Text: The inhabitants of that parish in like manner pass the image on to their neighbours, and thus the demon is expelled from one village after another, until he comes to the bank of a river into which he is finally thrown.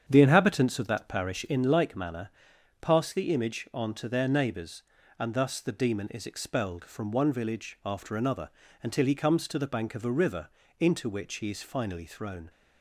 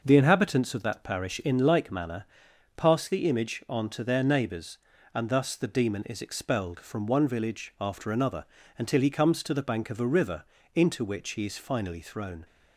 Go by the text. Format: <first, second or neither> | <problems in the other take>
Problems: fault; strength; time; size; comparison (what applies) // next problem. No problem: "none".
second | starts louder than the rest; strong; until 1.5 s; 8 dB // pauses between "manner" and "pass"; noticeable; at 2.2 s; 0.50 s long; noticeable in the second // pauses between "river" and "into"; slight; at 10.4 s; 0.32 s long; slight in the second